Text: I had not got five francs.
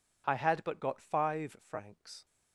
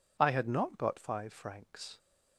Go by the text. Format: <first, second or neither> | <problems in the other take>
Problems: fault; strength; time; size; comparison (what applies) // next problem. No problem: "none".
second | says "but" for "not"; at 0.6 s